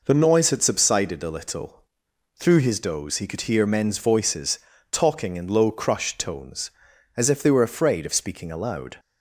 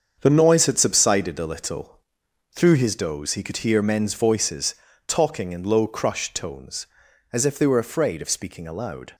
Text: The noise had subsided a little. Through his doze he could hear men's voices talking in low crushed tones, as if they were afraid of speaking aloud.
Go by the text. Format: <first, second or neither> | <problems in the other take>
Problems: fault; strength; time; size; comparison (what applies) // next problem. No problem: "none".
first | gets quieter; strong; throughout; 8 dB // pauses between "voices" and "talking"; slight; at 4.7 s; 0.32 s long; slight in the first